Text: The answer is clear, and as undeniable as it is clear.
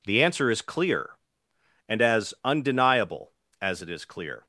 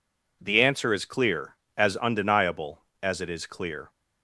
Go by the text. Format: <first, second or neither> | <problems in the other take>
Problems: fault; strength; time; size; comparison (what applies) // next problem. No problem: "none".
first | skips "and"; at 1.6 s